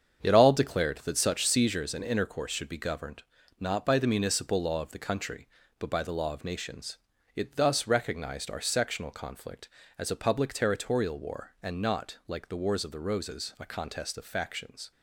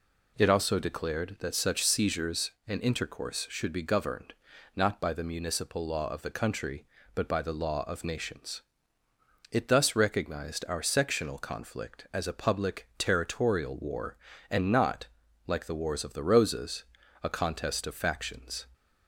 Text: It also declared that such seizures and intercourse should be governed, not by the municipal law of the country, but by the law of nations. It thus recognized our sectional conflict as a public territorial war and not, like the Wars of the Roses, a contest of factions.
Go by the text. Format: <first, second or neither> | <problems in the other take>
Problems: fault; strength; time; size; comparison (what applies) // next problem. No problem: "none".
second | starts louder than the rest; strong; until 1.2 s; 7.5 dB // says "all" for "also"; at 0.3 s